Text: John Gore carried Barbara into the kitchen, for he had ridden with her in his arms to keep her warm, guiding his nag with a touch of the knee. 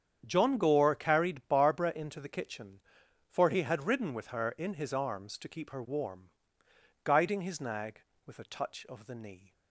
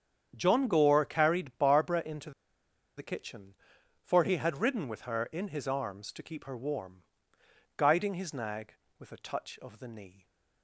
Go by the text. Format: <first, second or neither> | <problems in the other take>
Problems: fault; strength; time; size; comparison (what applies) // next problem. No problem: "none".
first | starts louder than the rest; strong; until 1.3 s; 8 dB; strong in the first // pauses between "into" and "the"; noticeable; at 2.3 s; 0.66 s long